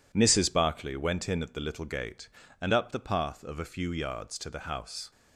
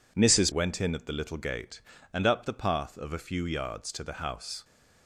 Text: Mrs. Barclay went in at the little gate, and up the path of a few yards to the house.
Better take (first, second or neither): first